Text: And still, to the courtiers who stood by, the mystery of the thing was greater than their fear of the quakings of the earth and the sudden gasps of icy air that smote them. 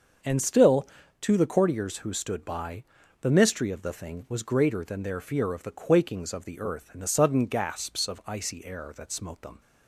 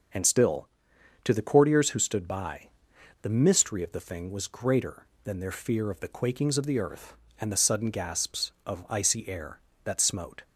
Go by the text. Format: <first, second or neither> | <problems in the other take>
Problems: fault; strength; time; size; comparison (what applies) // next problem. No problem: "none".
first | starts louder than the rest; noticeable; until 1.6 s; 6 dB; also in the first // stops before "them"; at 10.4 s